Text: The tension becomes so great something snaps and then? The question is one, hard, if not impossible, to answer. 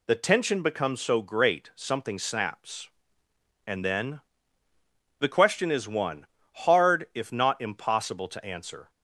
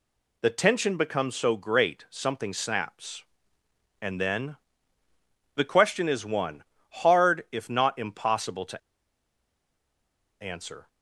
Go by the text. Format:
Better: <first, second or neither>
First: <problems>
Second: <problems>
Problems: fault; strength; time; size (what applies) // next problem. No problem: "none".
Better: first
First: none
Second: pauses between "to" and "answer"; strong; at 8.7 s; 1.6 s long